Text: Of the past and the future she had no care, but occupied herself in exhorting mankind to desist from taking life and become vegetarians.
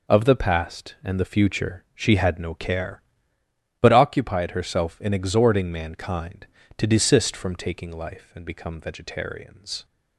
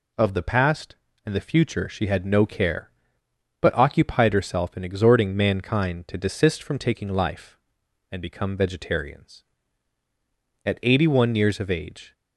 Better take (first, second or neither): first